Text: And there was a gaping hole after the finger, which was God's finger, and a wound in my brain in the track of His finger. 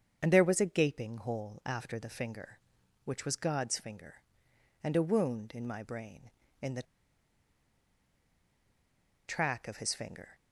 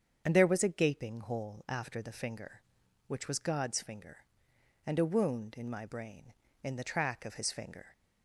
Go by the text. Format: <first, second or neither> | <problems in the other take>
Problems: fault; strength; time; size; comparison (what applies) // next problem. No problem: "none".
second | starts louder than the rest; until 1.2 s; 7 dB; strong in the second // pauses between "the" and "track"; strong; at 6.8 s; 2.4 s long